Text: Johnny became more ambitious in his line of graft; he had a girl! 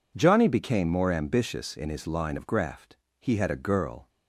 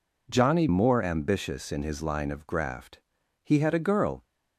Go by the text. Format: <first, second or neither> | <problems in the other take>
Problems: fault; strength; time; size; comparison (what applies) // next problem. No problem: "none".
first | skips "became"; at 0.6 s